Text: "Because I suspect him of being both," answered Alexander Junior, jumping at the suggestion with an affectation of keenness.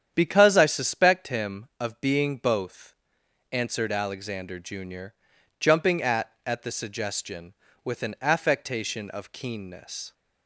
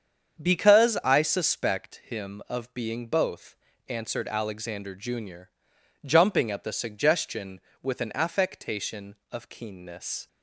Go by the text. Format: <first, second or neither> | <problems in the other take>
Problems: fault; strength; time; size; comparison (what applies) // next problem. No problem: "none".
second | starts louder than the rest; strong; until 1.1 s; 9 dB; strong in the second // says "at" twice; at 6.4 s